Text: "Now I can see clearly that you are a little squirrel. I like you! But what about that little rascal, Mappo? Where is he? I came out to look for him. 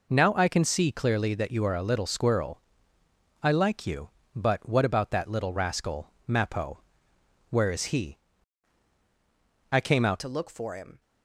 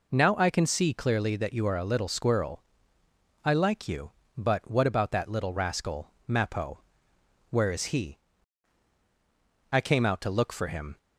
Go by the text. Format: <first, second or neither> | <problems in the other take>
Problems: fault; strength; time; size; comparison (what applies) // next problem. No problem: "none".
second | changes voice at "to"; from 10.2 s on; 0.8 s long